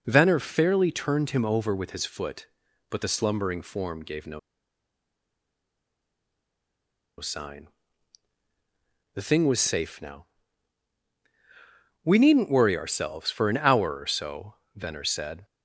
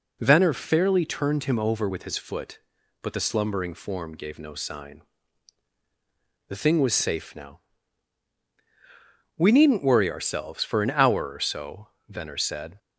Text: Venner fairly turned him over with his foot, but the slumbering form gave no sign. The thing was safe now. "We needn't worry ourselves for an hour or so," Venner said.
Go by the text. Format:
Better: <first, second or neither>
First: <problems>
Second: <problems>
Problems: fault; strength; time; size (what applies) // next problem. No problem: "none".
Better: second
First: pauses between "no" and "sign"; strong; at 4.3 s; 2.8 s long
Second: none